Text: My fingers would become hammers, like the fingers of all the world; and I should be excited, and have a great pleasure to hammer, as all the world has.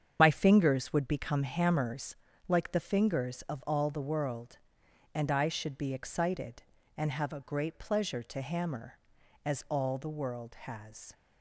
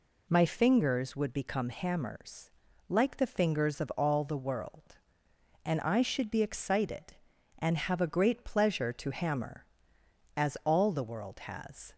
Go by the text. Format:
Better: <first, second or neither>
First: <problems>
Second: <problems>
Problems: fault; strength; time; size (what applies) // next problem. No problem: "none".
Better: second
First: loses the start of "My"; at 0.1 s; 50 ms // starts louder than the rest; strong; until 1.2 s; 8 dB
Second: none